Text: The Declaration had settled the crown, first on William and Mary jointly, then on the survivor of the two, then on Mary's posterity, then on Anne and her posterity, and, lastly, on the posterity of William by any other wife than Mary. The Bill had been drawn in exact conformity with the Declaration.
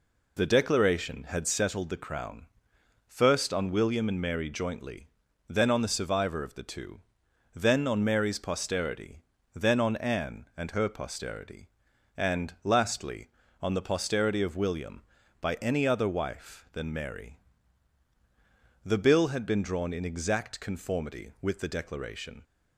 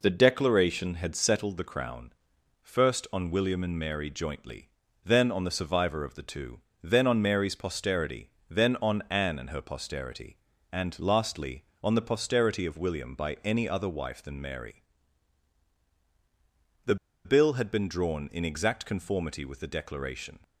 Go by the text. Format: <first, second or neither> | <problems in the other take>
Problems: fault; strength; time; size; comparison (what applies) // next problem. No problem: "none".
first | pauses between "The" and "Bill"; slight; at 16.9 s; 0.29 s long